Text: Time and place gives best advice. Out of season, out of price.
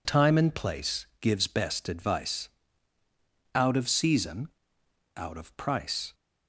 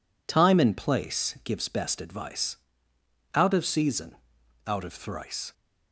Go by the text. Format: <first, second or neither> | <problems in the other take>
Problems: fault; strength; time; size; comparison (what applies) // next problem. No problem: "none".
first | says "thrice" for "price"; at 4.9 s